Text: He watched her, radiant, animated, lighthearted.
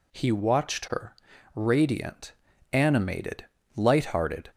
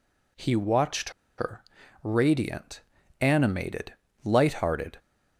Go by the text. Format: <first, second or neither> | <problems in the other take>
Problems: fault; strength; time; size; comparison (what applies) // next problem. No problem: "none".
first | pauses between "watched" and "her"; slight; at 1.1 s; 0.27 s long